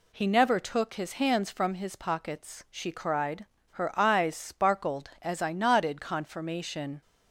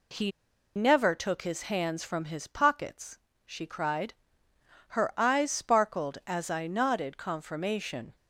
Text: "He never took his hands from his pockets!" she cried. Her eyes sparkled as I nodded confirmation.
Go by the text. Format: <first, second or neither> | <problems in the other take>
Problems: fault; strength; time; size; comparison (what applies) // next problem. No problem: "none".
first | pauses between "He" and "never"; at 0.2 s; 0.45 s long